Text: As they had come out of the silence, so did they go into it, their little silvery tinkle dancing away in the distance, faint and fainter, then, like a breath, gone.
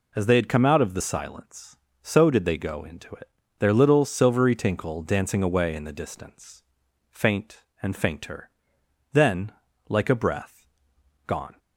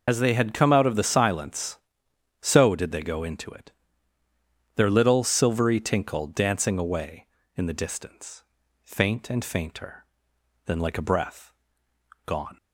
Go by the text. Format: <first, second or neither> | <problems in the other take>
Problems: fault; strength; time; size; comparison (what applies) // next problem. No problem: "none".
first | loses the start of "As"; at 0.0 s; 90 ms